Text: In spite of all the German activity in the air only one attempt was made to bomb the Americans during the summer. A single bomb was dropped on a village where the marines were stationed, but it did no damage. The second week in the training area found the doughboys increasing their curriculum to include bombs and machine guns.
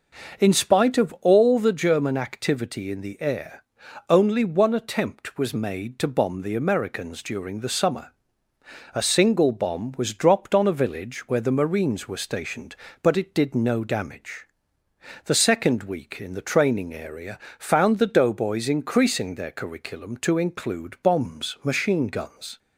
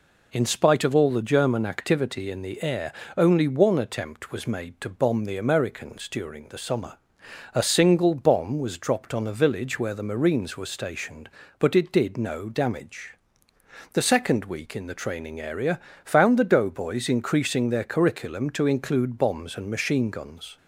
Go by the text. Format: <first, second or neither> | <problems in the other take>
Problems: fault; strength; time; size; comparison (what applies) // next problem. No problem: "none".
second | pauses between "air" and "only"; noticeable; at 3.6 s; 0.46 s long; slight in the second // pauses between "area" and "found"; slight; at 17.4 s; 0.18 s long; slight in the second // skips "and"; at 21.6 s